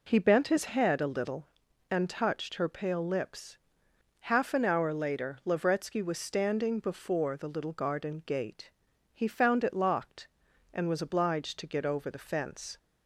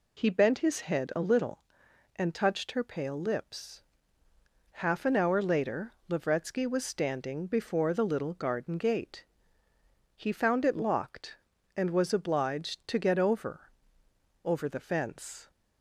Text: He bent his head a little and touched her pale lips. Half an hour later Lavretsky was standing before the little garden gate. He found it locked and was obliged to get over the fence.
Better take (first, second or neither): first